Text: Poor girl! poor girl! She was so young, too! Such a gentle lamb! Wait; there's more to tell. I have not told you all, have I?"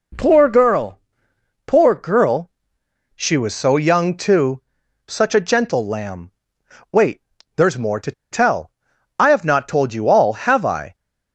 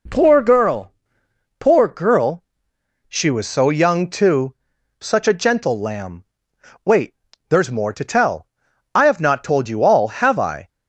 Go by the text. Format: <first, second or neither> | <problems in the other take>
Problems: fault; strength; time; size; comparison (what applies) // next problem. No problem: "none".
second | pauses between "to" and "tell"; slight; at 8.1 s; 0.20 s long